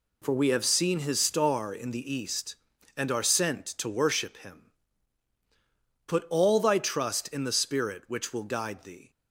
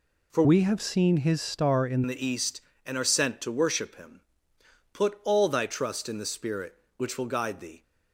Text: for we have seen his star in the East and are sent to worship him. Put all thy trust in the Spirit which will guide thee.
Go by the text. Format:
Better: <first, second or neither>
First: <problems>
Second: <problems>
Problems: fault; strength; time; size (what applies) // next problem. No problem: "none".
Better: first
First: none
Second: changes voice from "we" to "in"; from 0.4 to 2.0 s; 1.6 s long